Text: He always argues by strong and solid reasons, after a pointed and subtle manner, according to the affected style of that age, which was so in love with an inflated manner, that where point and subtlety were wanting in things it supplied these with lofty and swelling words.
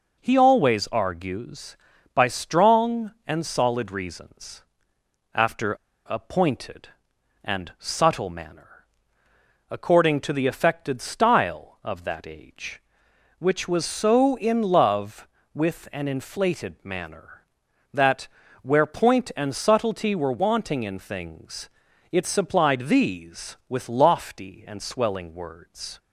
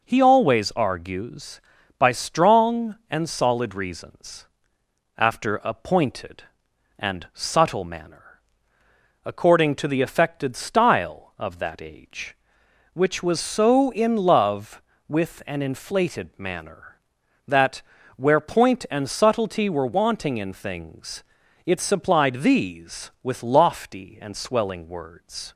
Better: second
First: pauses between "after" and "a"; slight; at 5.7 s; 0.31 s long // pauses between "that" and "where"; slight; at 18.2 s; 0.34 s long // pauses between "things" and "it"; at 21.6 s; 0.44 s long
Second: pauses between "that" and "where"; slight; at 17.8 s; 0.34 s long // pauses between "things" and "it"; at 21.2 s; 0.44 s long

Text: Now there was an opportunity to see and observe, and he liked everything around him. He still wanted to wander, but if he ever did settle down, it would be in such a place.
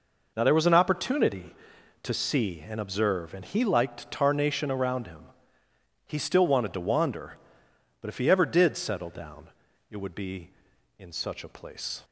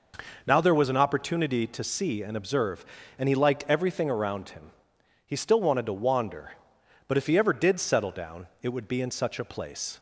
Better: second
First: says "tarnation" for "everything"; at 4.0 s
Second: none

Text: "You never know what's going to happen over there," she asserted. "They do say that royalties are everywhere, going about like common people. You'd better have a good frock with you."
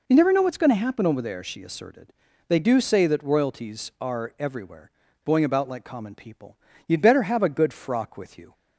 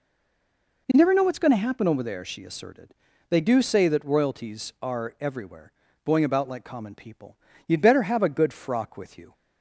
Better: first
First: none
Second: stays silent before the first word; slight; until 0.8 s; 0.8 s long

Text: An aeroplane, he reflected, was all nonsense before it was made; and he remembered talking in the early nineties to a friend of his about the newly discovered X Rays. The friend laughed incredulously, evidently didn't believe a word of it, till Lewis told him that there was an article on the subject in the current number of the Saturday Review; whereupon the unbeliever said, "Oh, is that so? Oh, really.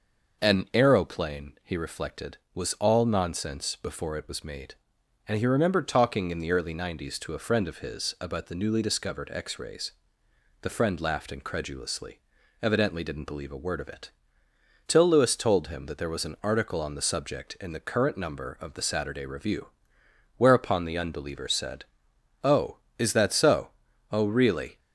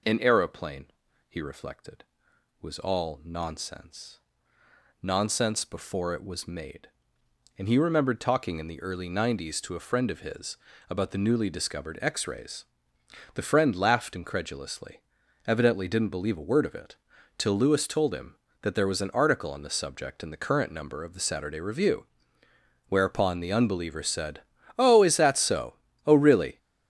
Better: first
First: none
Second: says "nonsense" twice; at 5.0 s // pauses between "his" and "about"; slight; at 10.5 s; 0.32 s long

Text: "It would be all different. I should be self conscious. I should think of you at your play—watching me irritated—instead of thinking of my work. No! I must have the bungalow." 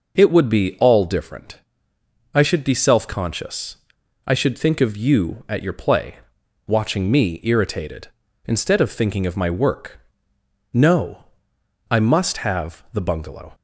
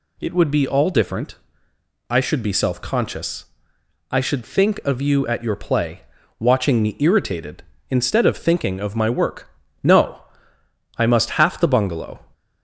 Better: first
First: none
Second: says "half" for "have"; at 11.3 s

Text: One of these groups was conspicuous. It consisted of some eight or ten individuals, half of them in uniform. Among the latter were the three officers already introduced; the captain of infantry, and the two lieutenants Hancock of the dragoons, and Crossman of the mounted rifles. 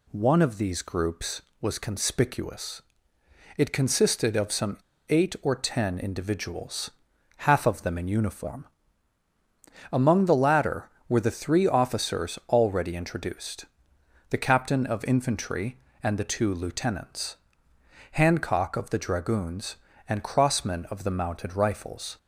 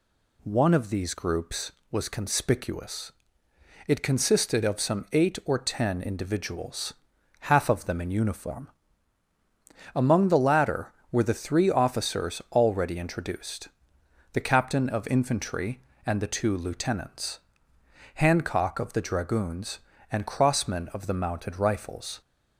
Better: second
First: pauses between "some" and "eight"; slight; at 4.7 s; 0.29 s long // pauses between "lieutenants" and "Hancock"; noticeable; at 17.3 s; 0.78 s long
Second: pauses between "lieutenants" and "Hancock"; noticeable; at 17.3 s; 0.78 s long

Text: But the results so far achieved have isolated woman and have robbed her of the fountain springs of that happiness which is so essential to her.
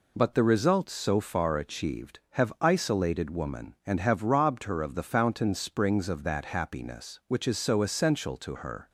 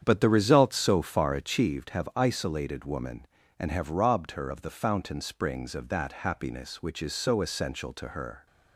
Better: first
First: none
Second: starts louder than the rest; strong; until 1.8 s; 8.5 dB

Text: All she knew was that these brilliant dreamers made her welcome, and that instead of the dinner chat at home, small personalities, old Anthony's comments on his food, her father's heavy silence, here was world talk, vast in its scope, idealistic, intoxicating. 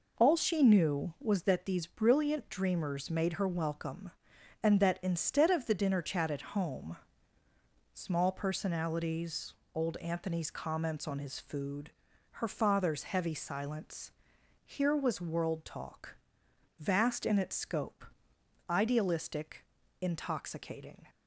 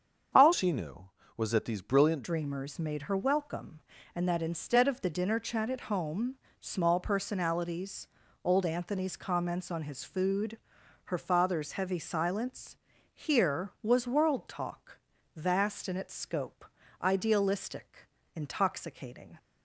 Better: first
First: none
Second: starts louder than the rest; until 1.6 s; 7 dB // changes voice from "she" to "brilliant"; from 0.5 to 2.2 s; 1.7 s long

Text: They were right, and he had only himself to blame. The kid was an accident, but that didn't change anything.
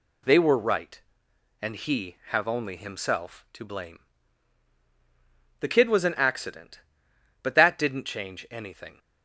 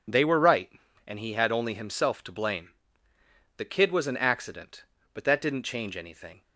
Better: second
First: says "have" for "had"; at 2.2 s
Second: none

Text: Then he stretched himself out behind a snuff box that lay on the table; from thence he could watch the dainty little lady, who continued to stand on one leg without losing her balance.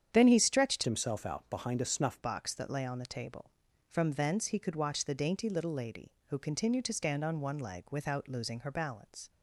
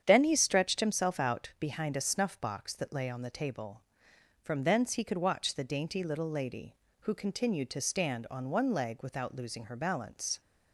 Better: second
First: starts louder than the rest; strong; until 1.1 s; 9 dB // changes voice from "himself" to "snuff"; from 0.8 to 2.2 s; 1.4 s long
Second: starts louder than the rest; strong; until 1.0 s; 8.5 dB

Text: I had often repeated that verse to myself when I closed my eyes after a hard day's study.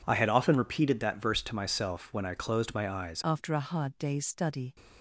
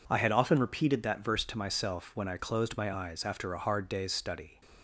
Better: second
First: changes voice at "after"; from 3.2 s on; 1.5 s long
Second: none

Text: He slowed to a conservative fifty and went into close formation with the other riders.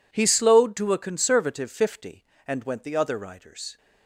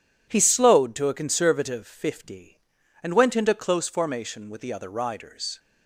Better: second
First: skips "into close formation with"; at 2.8 s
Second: none

